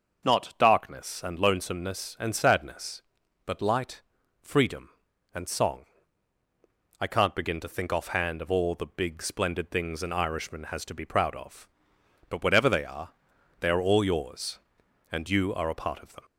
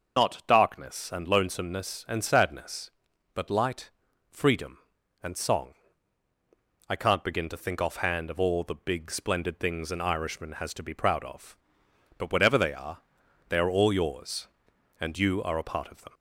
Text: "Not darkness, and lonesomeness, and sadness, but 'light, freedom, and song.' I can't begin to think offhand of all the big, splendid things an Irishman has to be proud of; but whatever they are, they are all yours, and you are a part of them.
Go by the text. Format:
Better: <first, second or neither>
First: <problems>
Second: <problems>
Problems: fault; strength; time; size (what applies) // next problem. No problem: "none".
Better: first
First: starts louder than the rest; until 1.3 s; 6.5 dB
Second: loses the start of "Not"; at 0.1 s; 30 ms // starts louder than the rest; until 1.2 s; 6 dB